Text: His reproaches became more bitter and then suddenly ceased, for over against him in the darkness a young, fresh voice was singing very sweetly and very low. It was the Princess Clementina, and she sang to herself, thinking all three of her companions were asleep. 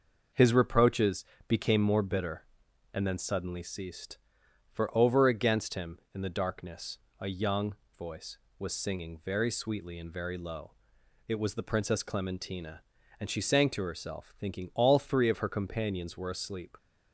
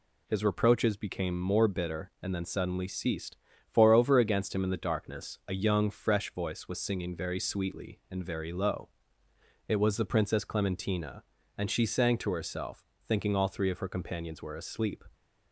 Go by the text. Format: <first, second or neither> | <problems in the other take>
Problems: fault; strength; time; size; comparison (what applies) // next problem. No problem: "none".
second | pauses between "reproaches" and "became"; slight; at 1.2 s; 0.22 s long // pauses between "darkness" and "a"; slight; at 6.9 s; 0.22 s long // skips "fresh"; at 7.8 s